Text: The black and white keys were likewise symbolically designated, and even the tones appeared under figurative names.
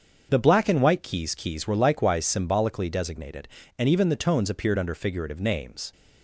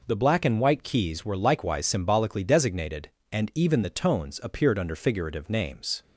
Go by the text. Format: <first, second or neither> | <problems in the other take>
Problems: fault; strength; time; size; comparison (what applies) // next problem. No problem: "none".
second | starts louder than the rest; until 1.3 s; 7 dB // says "keys" twice; at 1.3 s